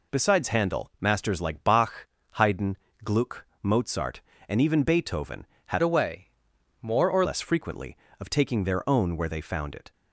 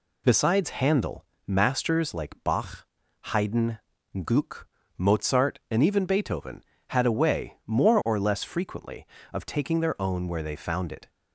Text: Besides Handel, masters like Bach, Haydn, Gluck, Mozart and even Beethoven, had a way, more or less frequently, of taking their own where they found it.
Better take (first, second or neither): second